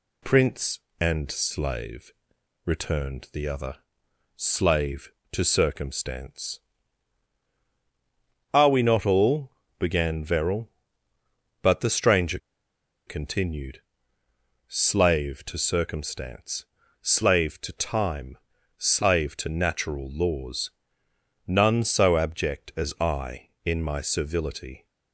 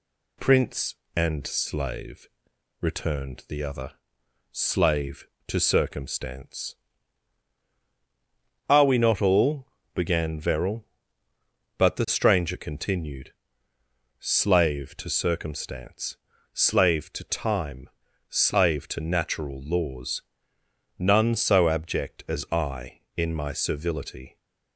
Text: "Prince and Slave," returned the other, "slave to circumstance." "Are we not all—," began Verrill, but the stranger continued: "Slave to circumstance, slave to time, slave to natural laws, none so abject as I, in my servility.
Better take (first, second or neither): second